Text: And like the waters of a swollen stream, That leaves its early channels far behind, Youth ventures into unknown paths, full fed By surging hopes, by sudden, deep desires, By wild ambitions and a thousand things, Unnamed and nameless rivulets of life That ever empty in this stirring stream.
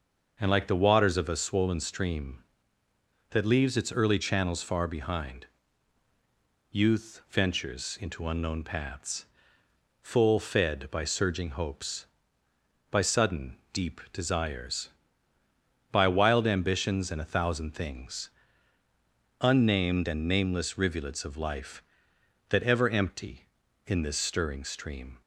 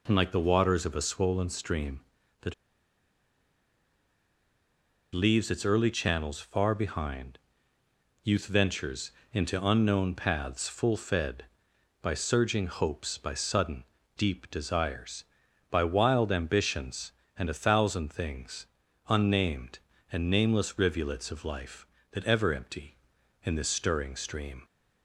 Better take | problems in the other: first | pauses between "That" and "leaves"; strong; at 2.5 s; 2.5 s long // pauses between "ventures" and "into"; slight; at 9.1 s; 0.22 s long

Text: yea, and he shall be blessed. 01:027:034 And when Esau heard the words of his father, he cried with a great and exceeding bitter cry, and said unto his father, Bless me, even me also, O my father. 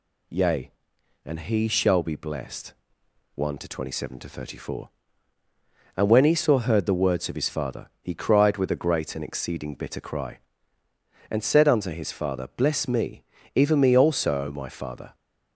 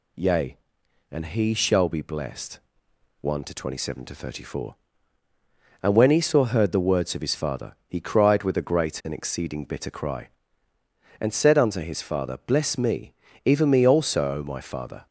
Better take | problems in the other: neither | none

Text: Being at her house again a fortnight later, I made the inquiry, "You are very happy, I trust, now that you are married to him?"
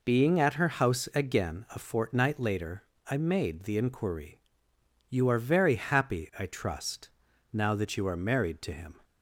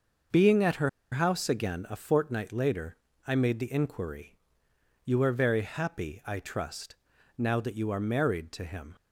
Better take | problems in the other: first | starts louder than the rest; until 1.5 s; 6 dB // pauses between "her" and "house"; slight; at 0.8 s; 0.23 s long

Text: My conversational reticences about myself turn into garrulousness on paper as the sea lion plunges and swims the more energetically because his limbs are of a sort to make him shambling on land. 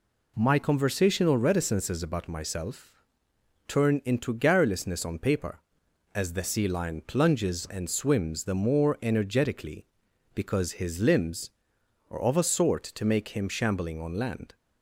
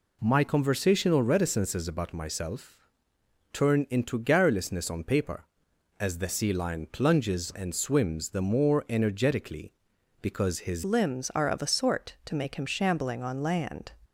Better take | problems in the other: first | pauses between "myself" and "turn"; noticeable; at 2.7 s; 0.78 s long; noticeable in the first // changes voice at "limbs"; from 10.8 s on; 3.1 s long

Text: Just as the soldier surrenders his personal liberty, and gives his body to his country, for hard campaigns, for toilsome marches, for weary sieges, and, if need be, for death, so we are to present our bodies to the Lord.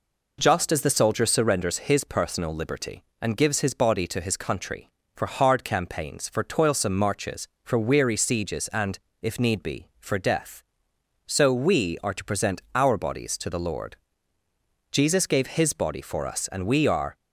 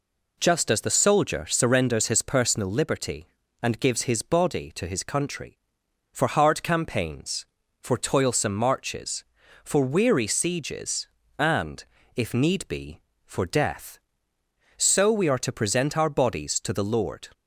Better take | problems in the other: second | goes on to say "Jesus gave His body for us and we are"; strong; from 14.9 s on; 2.2 s long

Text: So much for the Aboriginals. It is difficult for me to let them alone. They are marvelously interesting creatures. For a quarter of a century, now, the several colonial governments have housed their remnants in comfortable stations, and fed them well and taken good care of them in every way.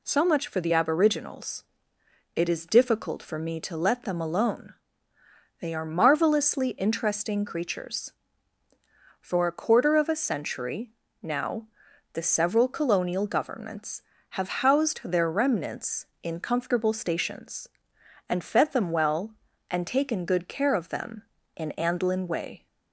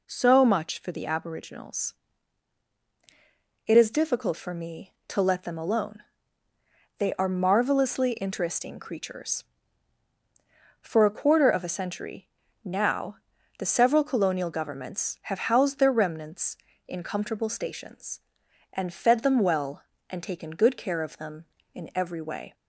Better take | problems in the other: second | says "andlin" for "every"; at 21.7 s

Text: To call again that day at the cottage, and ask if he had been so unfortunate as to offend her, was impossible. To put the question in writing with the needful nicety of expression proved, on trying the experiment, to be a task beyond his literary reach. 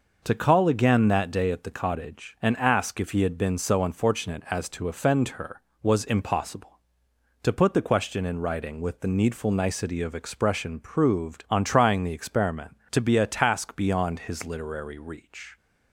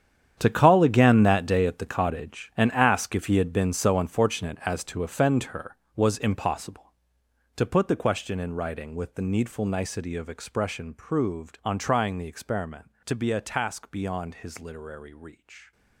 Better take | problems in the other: first | gets quieter; strong; throughout; 15 dB

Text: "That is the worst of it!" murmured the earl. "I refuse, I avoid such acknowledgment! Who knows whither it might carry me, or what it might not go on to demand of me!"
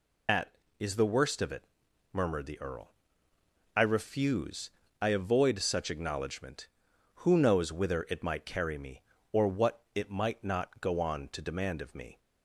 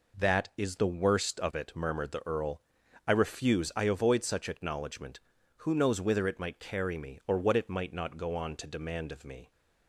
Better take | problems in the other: second | loses the start of "That"; at 0.2 s; 135 ms

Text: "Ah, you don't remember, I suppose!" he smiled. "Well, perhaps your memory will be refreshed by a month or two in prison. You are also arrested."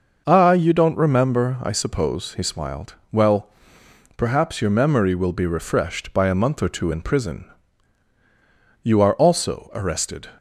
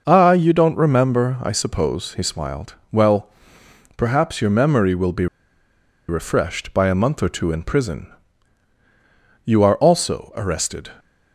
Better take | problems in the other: first | pauses between "be" and "refreshed"; noticeable; at 5.2 s; 0.82 s long

